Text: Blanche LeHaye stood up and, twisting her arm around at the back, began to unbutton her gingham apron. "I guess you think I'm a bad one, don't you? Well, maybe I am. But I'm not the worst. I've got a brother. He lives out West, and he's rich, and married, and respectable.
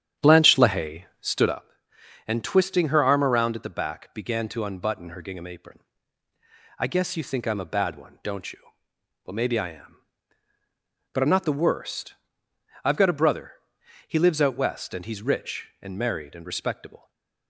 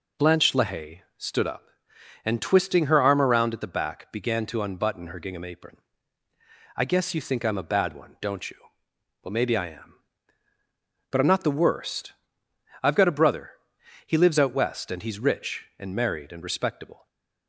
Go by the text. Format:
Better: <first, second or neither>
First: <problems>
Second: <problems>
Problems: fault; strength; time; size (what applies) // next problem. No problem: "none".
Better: second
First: starts louder than the rest; strong; until 1.7 s; 9.5 dB // pauses between "LeHaye" and "stood"; slight; at 1.0 s; 0.16 s long // stays silent after the last word; slight; from 16.9 s on; 0.5 s long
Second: pauses between "LeHaye" and "stood"; slight; at 1.0 s; 0.16 s long // stays silent after the last word; slight; from 16.9 s on; 0.5 s long